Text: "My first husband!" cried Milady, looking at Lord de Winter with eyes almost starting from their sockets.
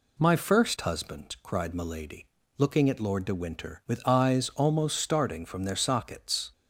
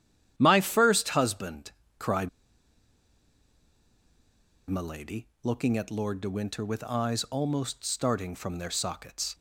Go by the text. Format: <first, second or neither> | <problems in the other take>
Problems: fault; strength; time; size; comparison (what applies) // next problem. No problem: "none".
first | starts louder than the rest; strong; until 1.3 s; 10.5 dB // pauses between "cried" and "Milady"; strong; at 2.2 s; 2.4 s long